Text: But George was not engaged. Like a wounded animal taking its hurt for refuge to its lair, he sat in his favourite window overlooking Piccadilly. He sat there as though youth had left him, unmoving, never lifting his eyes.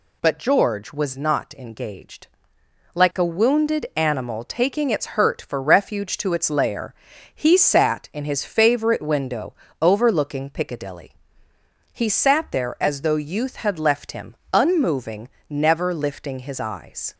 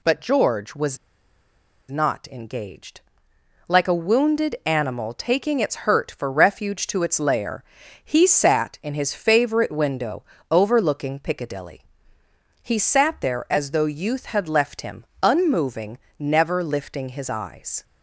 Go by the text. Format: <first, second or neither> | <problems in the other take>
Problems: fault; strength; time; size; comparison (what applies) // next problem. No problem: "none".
first | pauses between "was" and "not"; noticeable; at 0.9 s; 0.91 s long // pauses between "window" and "overlooking"; slight; at 10.2 s; 0.28 s long; slight in the first